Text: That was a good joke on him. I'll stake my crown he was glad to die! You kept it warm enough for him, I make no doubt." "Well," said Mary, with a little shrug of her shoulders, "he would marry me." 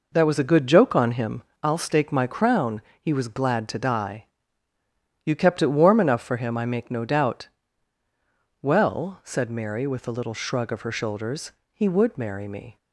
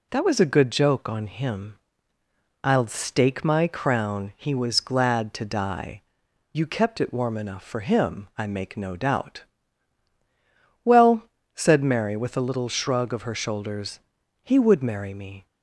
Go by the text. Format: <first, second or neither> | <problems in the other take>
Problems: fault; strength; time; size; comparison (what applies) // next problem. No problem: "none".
second | starts louder than the rest; noticeable; until 1.8 s; 4.5 dB // pauses between "crown" and "he"; slight; at 2.8 s; 0.20 s long